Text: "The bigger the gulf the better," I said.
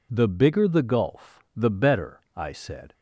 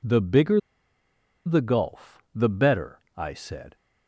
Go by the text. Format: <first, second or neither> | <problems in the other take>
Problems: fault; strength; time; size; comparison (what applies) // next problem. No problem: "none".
first | pauses between "bigger" and "the"; noticeable; at 0.5 s; 0.86 s long